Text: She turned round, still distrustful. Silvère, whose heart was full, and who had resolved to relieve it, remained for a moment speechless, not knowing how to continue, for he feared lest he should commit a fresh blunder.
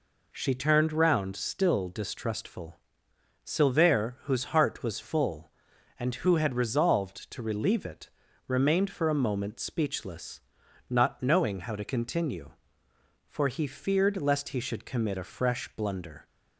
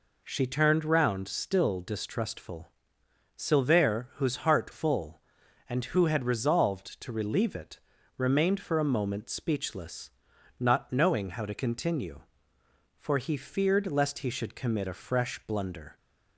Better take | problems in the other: first | skips "was"; at 4.7 s

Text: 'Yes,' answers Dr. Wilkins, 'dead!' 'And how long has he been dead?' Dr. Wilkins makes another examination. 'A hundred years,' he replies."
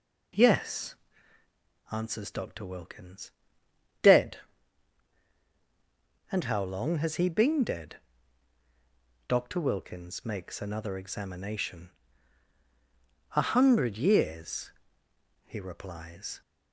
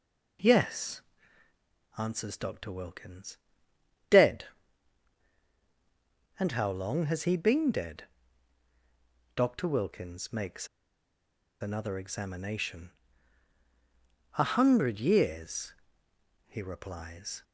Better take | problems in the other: first | pauses between "makes" and "another"; noticeable; at 10.6 s; 0.93 s long

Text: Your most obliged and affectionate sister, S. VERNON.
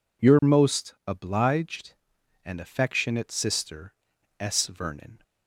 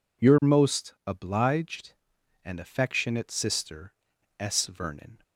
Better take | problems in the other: neither | none

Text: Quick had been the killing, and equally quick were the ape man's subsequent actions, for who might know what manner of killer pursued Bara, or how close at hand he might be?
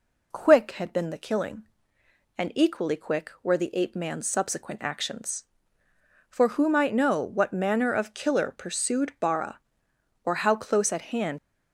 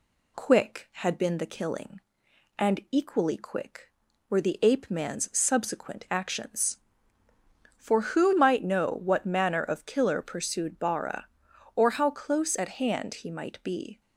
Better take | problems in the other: second | stops before "he might be"; at 11.3 s

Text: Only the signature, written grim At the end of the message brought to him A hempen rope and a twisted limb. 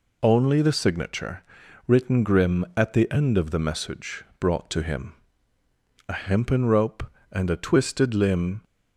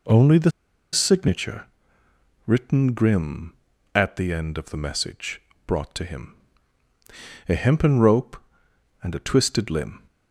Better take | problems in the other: first | pauses between "the" and "signature"; at 0.5 s; 0.42 s long // pauses between "message" and "brought"; slight; at 5.3 s; 0.26 s long; slight in the first // pauses between "him" and "A"; at 6.3 s; 1.1 s long; noticeable in the first

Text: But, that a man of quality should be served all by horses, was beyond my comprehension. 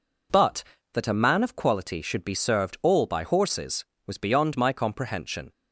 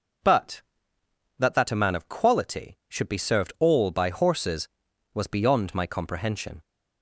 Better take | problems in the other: first | says "that" twice; at 1.5 s

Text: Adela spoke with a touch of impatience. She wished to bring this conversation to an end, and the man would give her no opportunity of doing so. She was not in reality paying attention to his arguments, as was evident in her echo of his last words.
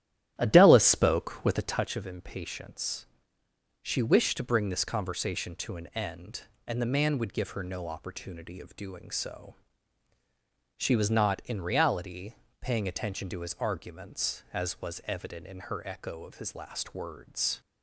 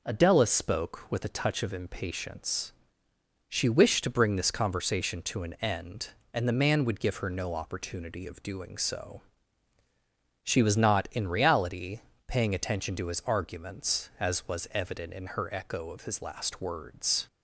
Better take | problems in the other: second | starts louder than the rest; strong; until 1.9 s; 12.5 dB // pauses between "reality" and "paying"; slight; at 12.3 s; 0.26 s long; slight in the second

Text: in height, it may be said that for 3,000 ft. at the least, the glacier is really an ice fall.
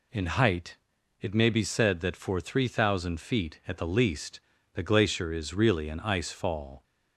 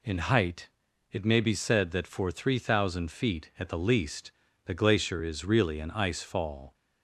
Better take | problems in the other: neither | none

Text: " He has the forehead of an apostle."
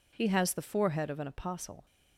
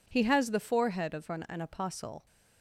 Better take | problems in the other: first | says "an" twice; at 1.4 s

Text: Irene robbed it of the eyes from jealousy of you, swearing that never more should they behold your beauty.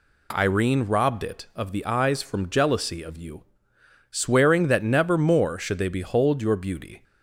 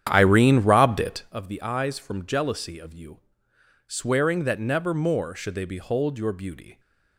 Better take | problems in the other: first | starts louder than the rest; strong; until 1.4 s; 9.5 dB

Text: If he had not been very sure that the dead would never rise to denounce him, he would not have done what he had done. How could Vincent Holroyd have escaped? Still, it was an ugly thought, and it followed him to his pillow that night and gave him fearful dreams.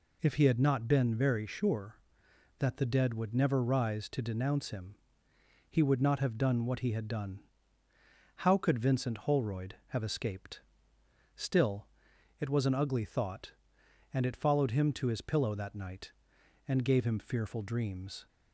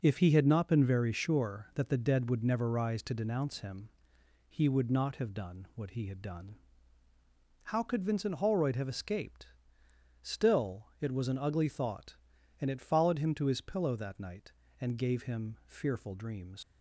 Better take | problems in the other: first | leaves "dreams" unfinished; at 16.6 s; 135 ms

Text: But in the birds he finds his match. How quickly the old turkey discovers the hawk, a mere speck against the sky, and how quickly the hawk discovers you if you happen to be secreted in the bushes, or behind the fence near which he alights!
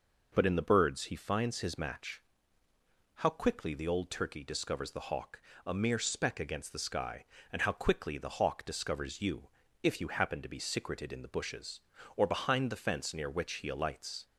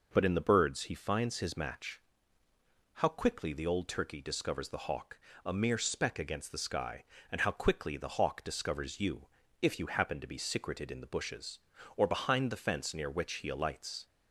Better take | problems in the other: neither | pauses between "you" and "if"; slight; the same in both

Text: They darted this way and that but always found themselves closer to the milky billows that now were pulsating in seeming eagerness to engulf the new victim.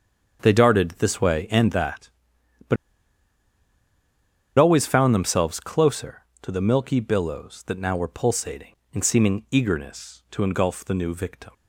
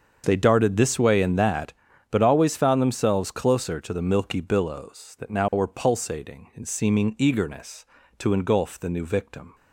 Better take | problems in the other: second | starts louder than the rest; strong; until 1.4 s; 7.5 dB; also in the second // pauses between "but" and "always"; strong; at 2.7 s; 1.8 s long

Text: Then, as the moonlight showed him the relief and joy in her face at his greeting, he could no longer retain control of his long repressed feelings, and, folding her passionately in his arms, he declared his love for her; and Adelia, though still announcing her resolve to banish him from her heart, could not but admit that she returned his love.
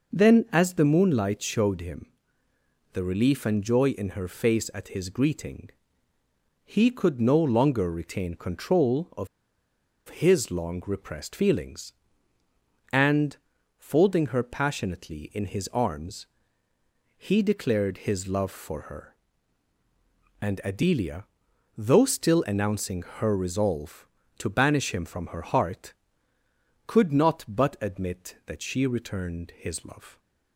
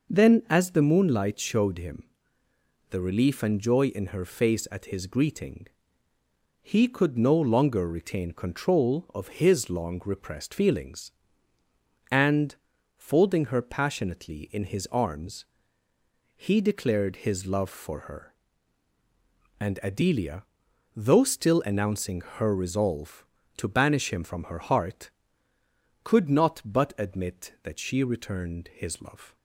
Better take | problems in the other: second | pauses between "him" and "the"; noticeable; at 2.0 s; 0.86 s long; noticeable in the second // pauses between "of" and "his"; noticeable; at 9.2 s; 0.81 s long // pauses between "announcing" and "her"; slight; at 23.0 s; 0.16 s long; slight in the second

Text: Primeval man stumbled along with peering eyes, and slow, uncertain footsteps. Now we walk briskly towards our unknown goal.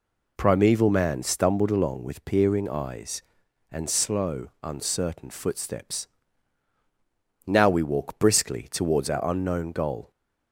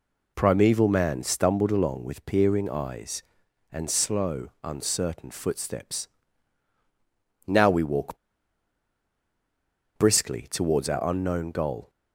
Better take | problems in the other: first | pauses between "walk" and "briskly"; strong; at 8.1 s; 1.8 s long

